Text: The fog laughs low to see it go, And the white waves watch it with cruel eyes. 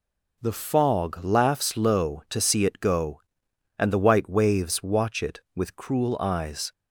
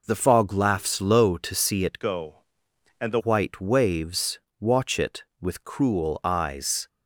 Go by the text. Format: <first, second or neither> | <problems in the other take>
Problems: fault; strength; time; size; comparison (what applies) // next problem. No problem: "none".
first | changes voice from "go" to "the"; from 2.0 to 3.1 s; 1.1 s long // pauses between "waves" and "watch"; slight; at 4.3 s; 0.18 s long